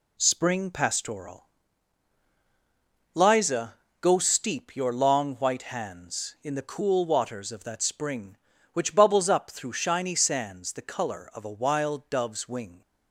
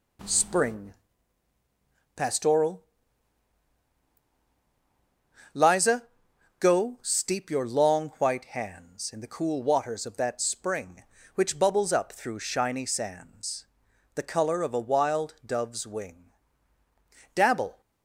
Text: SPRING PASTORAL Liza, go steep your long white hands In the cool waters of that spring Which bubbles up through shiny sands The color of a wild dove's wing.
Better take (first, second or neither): first